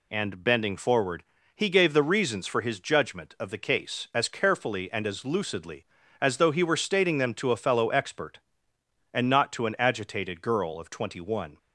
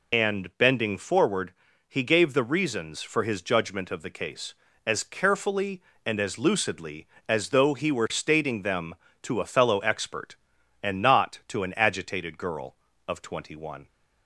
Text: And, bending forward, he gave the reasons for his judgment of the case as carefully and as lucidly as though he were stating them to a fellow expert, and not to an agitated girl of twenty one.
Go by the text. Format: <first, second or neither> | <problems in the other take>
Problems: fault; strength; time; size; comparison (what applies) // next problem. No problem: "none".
first | loses the start of "And"; at 0.1 s; 60 ms